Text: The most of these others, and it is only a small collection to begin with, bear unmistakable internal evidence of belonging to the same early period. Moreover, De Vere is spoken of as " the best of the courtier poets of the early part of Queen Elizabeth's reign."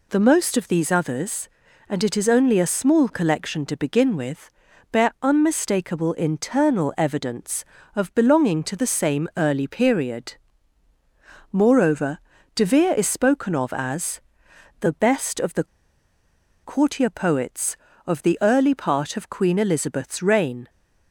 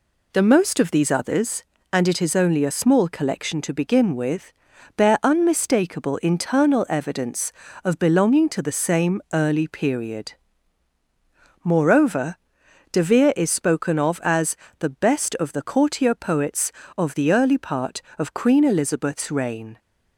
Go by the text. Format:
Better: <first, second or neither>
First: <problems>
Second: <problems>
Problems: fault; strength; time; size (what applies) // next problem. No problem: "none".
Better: second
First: pauses between "the" and "courtier"; at 15.6 s; 0.99 s long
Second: none